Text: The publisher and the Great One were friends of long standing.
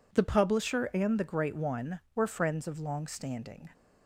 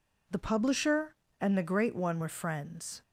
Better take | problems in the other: first | stops before "of long standing"; at 3.0 s

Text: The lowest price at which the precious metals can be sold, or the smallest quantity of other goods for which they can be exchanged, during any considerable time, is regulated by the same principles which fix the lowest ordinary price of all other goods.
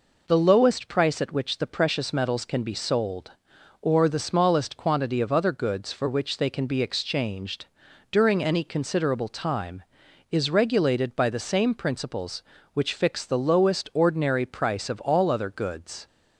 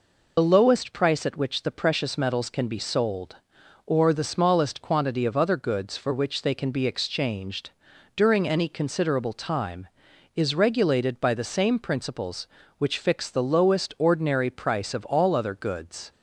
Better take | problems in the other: first | loses the start of "The"; at 0.3 s; 45 ms

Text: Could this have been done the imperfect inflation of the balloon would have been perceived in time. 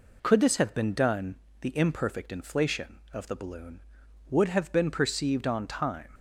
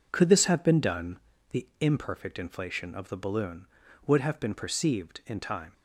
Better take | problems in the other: second | pauses between "done" and "the"; slight; at 1.3 s; 0.26 s long; slight in the second // says "on" for "in"; at 5.4 s

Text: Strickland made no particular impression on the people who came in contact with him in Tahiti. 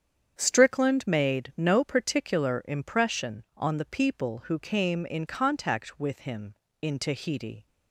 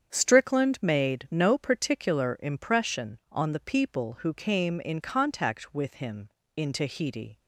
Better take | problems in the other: neither | starts louder than the rest; strong; the same in both

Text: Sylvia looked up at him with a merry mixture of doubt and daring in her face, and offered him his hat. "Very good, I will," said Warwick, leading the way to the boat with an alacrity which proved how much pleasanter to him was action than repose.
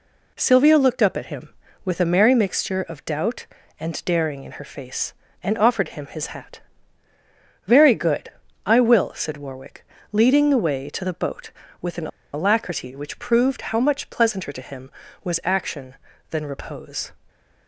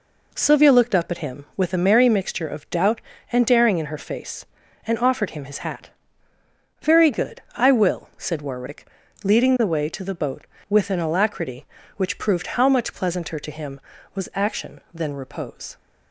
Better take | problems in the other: second | pauses between "an" and "alacrity"; slight; at 12.0 s; 0.26 s long

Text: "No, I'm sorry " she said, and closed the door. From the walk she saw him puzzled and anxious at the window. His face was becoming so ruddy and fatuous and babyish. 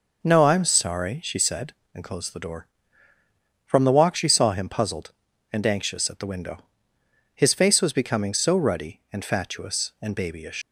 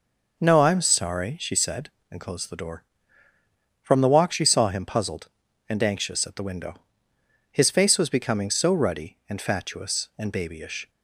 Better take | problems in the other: second | leaves "babyish" unfinished; at 10.6 s; 115 ms

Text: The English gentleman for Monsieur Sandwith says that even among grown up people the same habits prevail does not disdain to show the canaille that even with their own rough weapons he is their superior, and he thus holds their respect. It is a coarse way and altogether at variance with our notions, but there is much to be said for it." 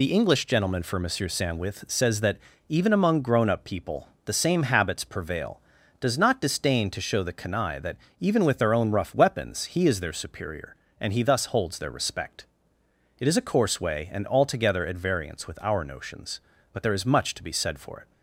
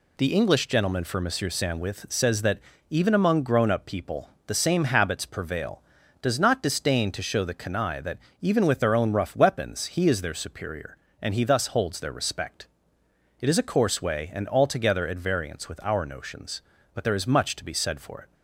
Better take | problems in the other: second | loses the start of "The"; at 0.0 s; 25 ms // pauses between "that" and "even"; slight; at 2.3 s; 0.32 s long; slight in the second // pauses between "people" and "the"; slight; at 4.0 s; 0.16 s long; slight in the second // pauses between "that" and "even"; slight; at 7.9 s; 0.20 s long; slight in the second

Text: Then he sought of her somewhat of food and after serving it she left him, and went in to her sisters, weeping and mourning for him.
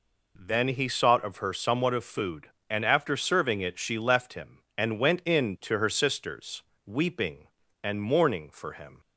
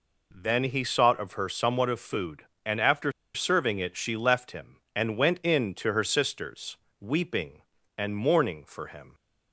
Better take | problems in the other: first | pauses between "after" and "serving"; slight; at 3.1 s; 0.22 s long

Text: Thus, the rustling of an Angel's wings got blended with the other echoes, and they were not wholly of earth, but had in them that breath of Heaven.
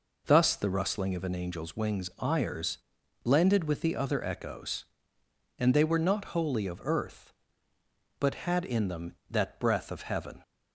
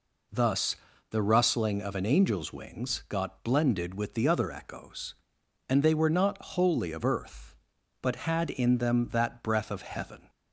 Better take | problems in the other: second | says "ires" for "got"; at 2.1 s

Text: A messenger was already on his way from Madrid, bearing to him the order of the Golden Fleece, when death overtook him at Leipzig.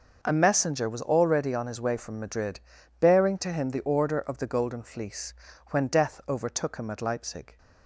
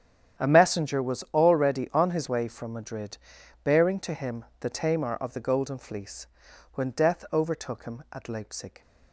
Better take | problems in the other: first | starts louder than the rest; strong; until 1.4 s; 9.5 dB // pauses between "him" and "the"; slight; at 4.4 s; 0.16 s long // says "tamar" for "order"; at 4.6 s

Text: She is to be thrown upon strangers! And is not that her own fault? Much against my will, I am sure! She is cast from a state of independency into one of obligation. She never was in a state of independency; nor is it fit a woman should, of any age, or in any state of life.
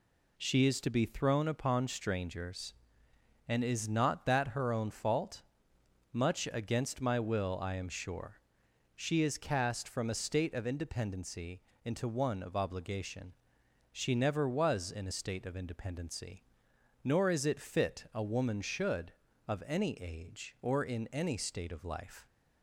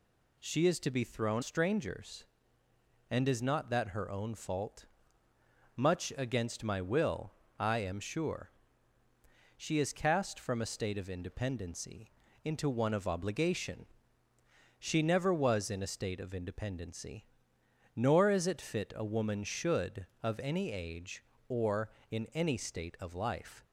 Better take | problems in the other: first | skips "upon"; at 1.4 s // pauses between "independency" and "into"; slight; at 12.1 s; 0.32 s long; slight in the first

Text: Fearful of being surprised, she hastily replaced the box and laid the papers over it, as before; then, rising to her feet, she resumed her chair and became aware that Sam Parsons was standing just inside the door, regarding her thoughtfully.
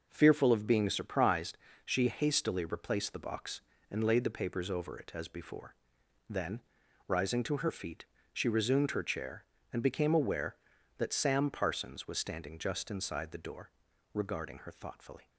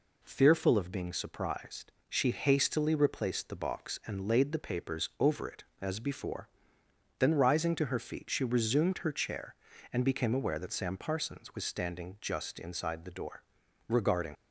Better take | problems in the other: first | stops before "her thoughtfully"; at 14.3 s

